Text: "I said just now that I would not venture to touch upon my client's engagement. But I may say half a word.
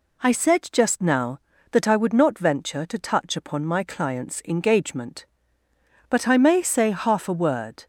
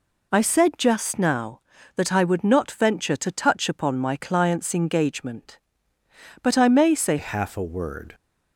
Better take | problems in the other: first | changes voice at "half"; from 7.1 s on; 1.0 s long

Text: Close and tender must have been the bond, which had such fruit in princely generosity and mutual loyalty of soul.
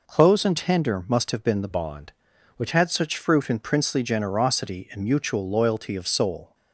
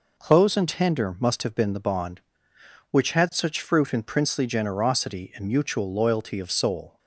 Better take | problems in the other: second | changes voice from "bond" to "which"; from 1.7 to 2.7 s; 1.0 s long

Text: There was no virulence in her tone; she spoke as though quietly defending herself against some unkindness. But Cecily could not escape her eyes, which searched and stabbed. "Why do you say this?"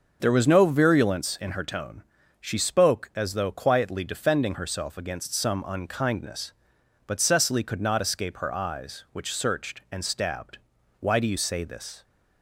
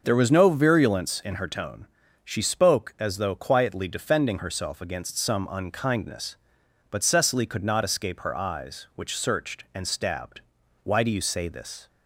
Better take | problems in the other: neither | starts louder than the rest; the same in both

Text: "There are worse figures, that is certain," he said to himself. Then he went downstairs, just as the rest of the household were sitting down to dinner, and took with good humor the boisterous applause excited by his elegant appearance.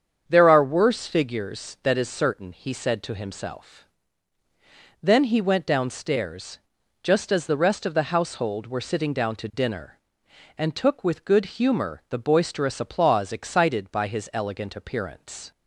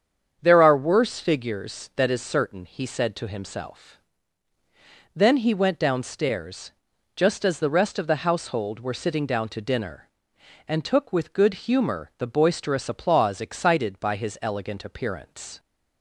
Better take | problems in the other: neither | starts louder than the rest; strong; the same in both

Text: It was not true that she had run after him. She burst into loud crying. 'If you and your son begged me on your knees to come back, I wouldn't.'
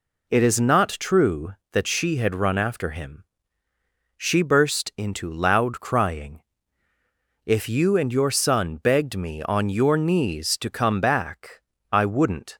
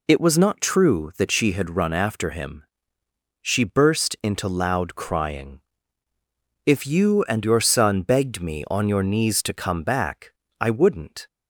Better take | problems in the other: second | says "is" for "was"; at 0.4 s

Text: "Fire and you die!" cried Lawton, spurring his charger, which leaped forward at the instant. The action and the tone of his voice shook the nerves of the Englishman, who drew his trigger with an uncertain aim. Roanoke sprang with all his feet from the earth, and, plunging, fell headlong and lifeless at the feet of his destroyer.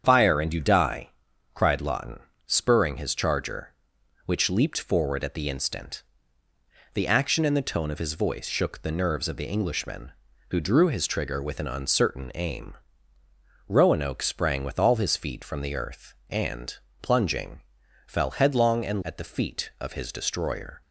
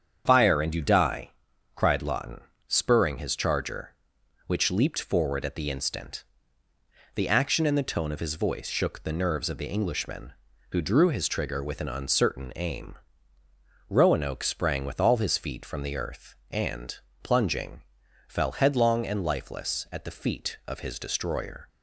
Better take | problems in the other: second | starts louder than the rest; strong; until 1.0 s; 8 dB; strong in the second // skips "lifeless"; at 19.0 s

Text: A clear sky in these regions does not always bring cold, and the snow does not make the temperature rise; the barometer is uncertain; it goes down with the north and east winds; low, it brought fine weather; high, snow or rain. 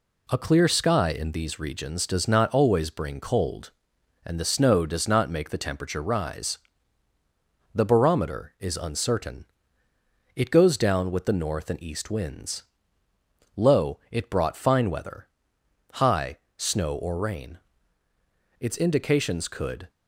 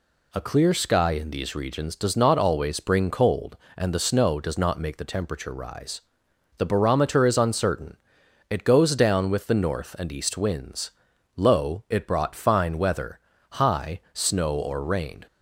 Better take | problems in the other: second | goes on to say "Its indications could"; from 18.5 s on; 1.3 s long

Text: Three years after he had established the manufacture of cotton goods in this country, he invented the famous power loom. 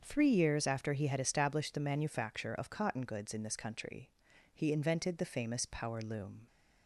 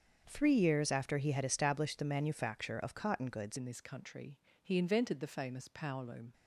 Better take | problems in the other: first | starts louder than the rest; until 1.2 s; 7 dB; also in the first // changes voice at "in"; from 3.5 s on; 2.8 s long

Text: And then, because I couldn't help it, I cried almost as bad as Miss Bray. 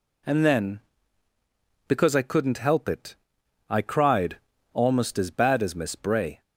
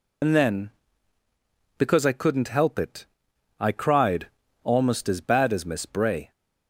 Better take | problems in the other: first | loses the start of "And"; at 0.2 s; 65 ms // pauses between "cried" and "almost"; slight; at 4.2 s; 0.36 s long; slight in the first

